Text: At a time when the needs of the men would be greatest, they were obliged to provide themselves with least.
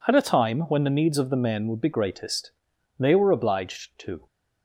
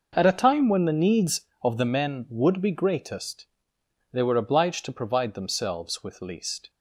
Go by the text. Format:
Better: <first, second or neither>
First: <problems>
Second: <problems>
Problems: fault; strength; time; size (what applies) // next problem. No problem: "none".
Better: second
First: stops before "provide themselves with least"; at 4.2 s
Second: none